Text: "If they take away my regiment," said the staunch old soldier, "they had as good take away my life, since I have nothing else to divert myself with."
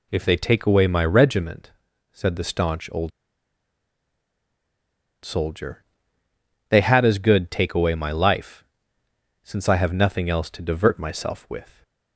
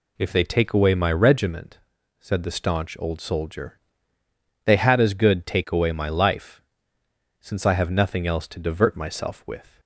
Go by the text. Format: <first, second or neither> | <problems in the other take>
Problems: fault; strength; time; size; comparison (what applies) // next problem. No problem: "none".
second | pauses between "old" and "soldier"; strong; at 3.1 s; 2.1 s long